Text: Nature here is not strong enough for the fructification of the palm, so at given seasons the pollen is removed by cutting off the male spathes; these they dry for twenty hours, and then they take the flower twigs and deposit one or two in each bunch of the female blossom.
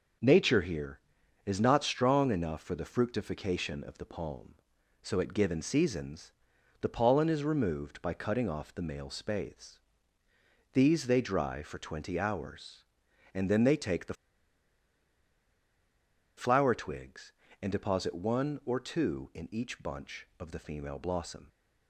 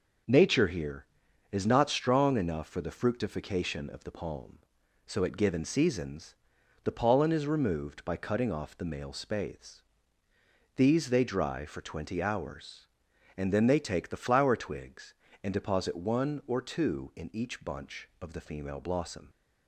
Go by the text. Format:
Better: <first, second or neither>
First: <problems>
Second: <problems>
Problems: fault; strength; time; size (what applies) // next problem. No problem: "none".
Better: second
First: pauses between "seasons" and "the"; noticeable; at 6.3 s; 0.48 s long // pauses between "the" and "flower"; strong; at 14.1 s; 2.2 s long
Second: pauses between "seasons" and "the"; noticeable; at 6.3 s; 0.48 s long